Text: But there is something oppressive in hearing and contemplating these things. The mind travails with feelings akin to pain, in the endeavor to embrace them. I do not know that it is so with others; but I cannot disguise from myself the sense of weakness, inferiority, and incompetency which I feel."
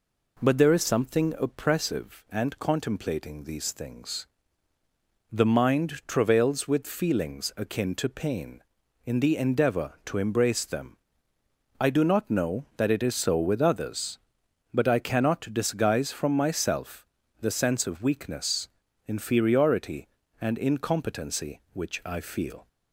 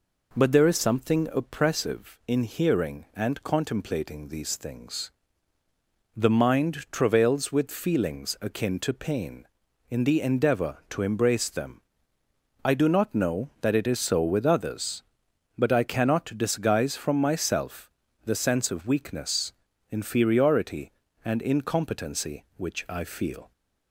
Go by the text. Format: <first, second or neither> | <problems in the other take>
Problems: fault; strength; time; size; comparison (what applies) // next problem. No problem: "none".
second | skips "in hearing"; at 2.2 s // pauses between "myself" and "the"; slight; at 17.0 s; 0.34 s long; slight in the second